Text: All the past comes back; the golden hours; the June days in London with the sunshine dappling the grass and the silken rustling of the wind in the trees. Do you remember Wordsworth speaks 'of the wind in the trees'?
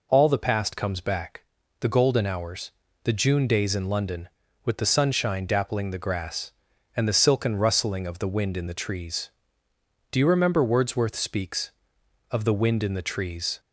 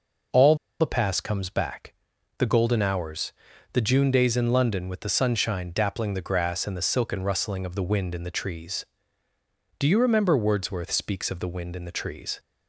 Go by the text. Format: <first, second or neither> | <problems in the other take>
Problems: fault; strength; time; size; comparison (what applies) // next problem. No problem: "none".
first | pauses between "All" and "the"; slight; at 0.5 s; 0.25 s long